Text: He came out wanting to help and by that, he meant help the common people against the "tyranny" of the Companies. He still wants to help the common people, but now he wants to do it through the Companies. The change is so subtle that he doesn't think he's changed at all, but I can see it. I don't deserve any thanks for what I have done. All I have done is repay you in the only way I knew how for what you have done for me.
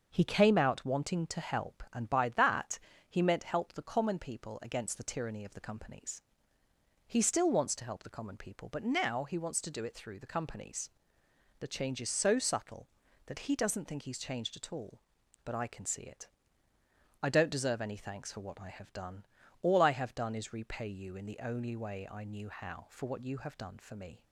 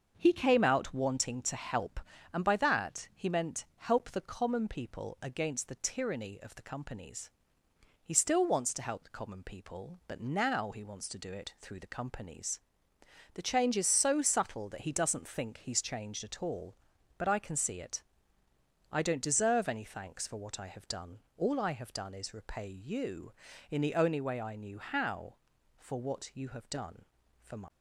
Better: first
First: starts louder than the rest; until 1.1 s; 6.5 dB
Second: starts louder than the rest; until 1.1 s; 6.5 dB // says "my" for "me"; at 27.5 s

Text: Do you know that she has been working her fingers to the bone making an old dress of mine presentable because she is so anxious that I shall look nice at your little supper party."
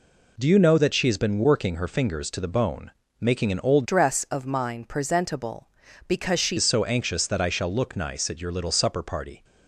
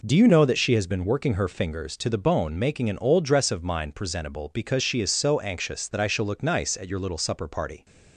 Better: second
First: pauses between "bone" and "making"; slight; at 2.9 s; 0.30 s long // changes voice from "dress" to "she"; from 3.8 to 6.5 s; 2.7 s long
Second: none

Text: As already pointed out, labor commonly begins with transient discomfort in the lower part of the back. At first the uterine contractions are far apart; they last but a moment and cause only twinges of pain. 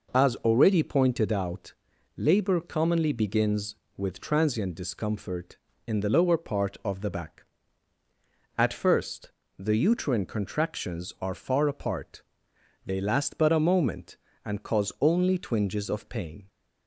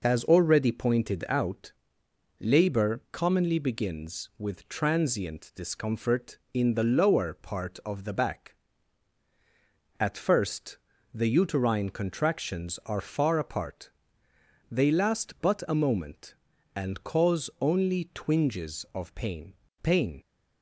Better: first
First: pauses between "first" and "the"; slight; at 9.3 s; 0.30 s long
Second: pauses between "first" and "the"; slight; at 10.7 s; 0.36 s long // says "pain" twice; at 19.8 s

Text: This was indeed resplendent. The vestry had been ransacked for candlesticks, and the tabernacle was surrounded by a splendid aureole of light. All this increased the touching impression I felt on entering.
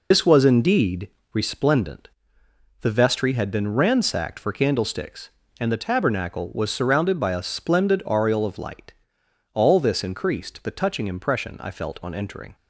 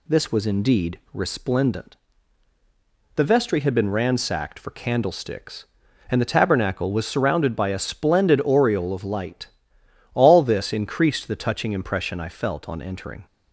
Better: second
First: loses the start of "This"; at 0.1 s; 75 ms // pauses between "indeed" and "resplendent"; slight; at 1.0 s; 0.24 s long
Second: pauses between "indeed" and "resplendent"; slight; at 0.9 s; 0.16 s long

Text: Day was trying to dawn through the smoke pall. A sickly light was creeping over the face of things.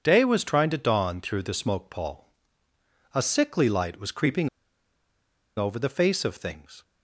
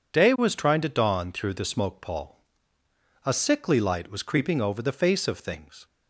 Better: second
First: pauses between "creeping" and "over"; at 4.4 s; 1.0 s long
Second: none

